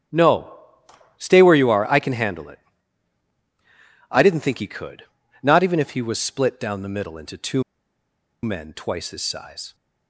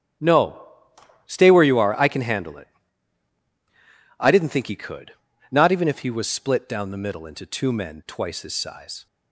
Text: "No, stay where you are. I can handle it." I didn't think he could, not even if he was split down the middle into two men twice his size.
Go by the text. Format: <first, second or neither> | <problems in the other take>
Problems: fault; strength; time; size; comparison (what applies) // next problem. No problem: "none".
second | starts louder than the rest; strong; until 1.7 s; 11.5 dB; strong in the second // pauses between "two" and "men"; noticeable; at 7.6 s; 0.81 s long